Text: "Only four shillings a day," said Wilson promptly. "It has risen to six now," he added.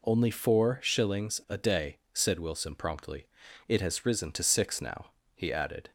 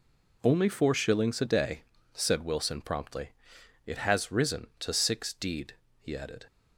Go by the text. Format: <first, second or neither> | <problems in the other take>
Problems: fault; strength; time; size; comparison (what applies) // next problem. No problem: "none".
first | says "deed" for "now"; at 5.3 s